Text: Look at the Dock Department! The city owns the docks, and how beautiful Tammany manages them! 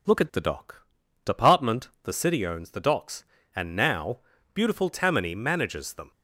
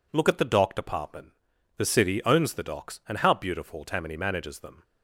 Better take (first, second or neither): second